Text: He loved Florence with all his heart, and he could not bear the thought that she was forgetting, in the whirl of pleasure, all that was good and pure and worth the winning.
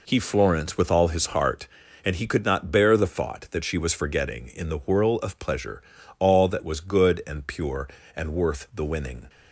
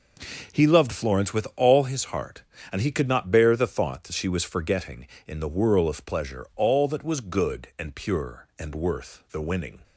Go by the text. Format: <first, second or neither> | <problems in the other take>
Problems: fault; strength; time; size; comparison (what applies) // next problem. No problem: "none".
second | skips "loved"; at 0.1 s